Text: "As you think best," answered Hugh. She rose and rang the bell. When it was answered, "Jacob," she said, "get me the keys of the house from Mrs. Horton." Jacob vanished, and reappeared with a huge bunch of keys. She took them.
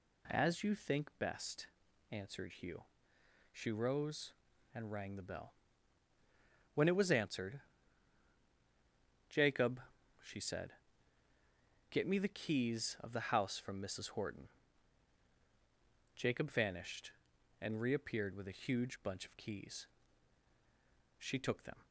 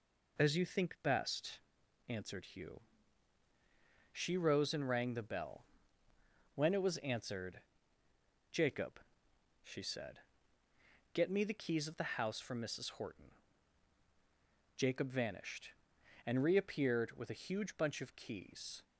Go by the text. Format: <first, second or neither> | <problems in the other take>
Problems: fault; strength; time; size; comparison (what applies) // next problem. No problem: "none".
first | stops before "She took them"; at 18.8 s